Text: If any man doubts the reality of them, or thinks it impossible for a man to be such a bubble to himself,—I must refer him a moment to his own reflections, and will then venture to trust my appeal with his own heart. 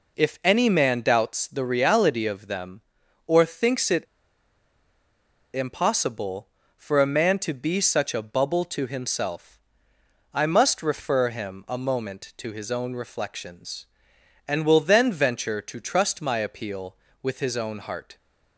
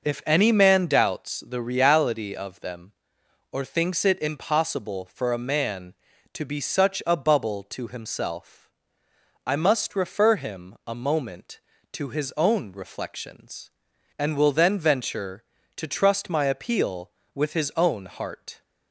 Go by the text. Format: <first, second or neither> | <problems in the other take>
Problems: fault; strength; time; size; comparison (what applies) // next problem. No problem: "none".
second | pauses between "it" and "impossible"; strong; at 4.0 s; 1.4 s long